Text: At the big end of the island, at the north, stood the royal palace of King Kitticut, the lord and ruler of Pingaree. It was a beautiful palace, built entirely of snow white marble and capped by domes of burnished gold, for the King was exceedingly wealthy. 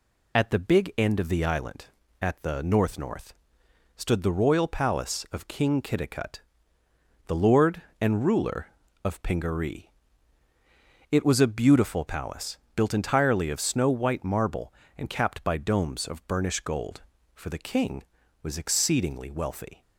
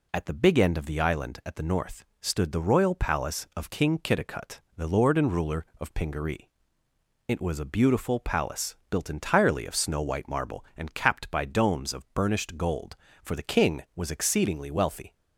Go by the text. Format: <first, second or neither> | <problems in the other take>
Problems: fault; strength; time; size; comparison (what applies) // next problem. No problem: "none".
second | says "north" twice; at 2.9 s